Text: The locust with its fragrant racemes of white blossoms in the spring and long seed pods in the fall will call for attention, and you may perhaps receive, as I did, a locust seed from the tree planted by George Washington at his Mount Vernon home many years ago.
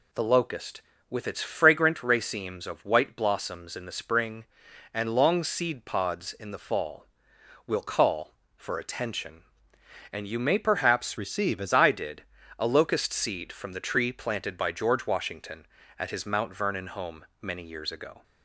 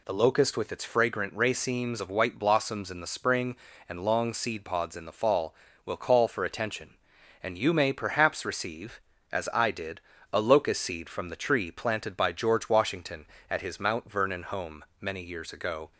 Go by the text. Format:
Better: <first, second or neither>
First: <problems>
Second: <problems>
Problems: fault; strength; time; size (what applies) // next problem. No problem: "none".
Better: second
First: changes voice from "receive" to "as"; from 11.1 to 11.7 s; 0.6 s long // pauses between "home" and "many"; slight; at 17.2 s; 0.16 s long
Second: pauses between "home" and "many"; slight; at 14.8 s; 0.16 s long